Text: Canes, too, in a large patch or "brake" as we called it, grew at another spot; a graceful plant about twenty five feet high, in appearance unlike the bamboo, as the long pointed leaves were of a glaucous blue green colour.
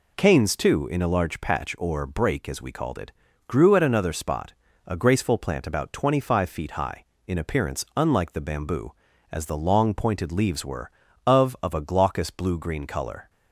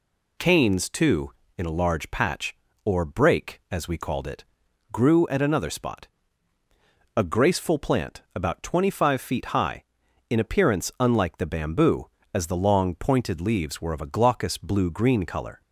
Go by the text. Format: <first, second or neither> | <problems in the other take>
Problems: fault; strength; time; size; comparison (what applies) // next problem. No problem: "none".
second | says "of" twice; at 11.6 s